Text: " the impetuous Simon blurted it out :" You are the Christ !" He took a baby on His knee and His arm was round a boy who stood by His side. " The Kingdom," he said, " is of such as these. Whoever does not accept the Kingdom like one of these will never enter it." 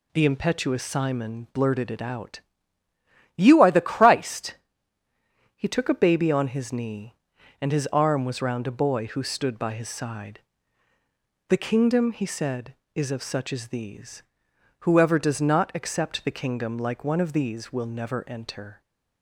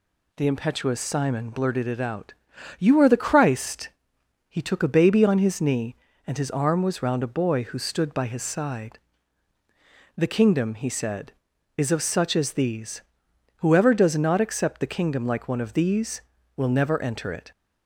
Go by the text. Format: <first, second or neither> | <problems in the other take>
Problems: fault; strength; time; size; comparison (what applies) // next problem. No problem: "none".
second | stops before "it"; at 18.8 s